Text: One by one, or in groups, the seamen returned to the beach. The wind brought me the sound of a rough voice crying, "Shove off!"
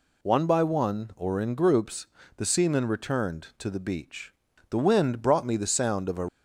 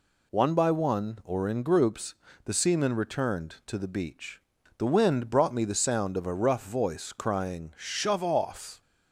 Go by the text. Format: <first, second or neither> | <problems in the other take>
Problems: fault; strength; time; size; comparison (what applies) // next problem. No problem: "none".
second | stops before "rough voice crying Shove off"; at 6.2 s